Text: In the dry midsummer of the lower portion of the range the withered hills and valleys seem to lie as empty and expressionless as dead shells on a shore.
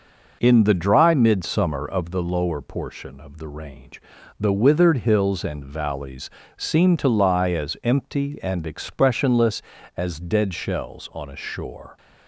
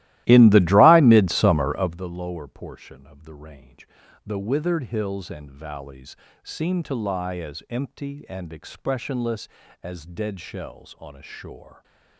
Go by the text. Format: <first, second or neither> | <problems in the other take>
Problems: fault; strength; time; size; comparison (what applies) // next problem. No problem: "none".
first | starts louder than the rest; strong; until 2.1 s; 16 dB // pauses between "range" and "the"; slight; at 3.8 s; 0.36 s long; slight in the first // pauses between "valleys" and "seem"; slight; at 6.1 s; 0.28 s long; slight in the first